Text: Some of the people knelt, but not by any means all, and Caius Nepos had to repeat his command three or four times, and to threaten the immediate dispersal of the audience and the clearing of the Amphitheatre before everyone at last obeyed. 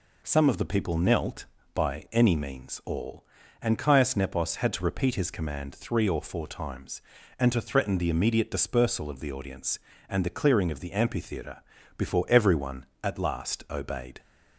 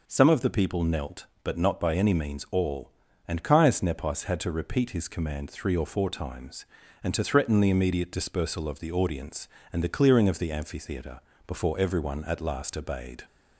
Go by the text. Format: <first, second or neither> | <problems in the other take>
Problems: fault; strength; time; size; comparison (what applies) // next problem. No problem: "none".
second | skips "but not"; at 1.6 s // pauses between "Amphitheatre" and "before"; slight; at 11.6 s; 0.36 s long; slight in the second